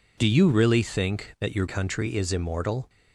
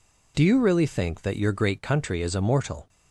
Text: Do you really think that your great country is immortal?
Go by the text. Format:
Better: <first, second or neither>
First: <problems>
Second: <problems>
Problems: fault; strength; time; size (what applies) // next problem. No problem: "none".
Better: second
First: skips "great"; at 1.6 s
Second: none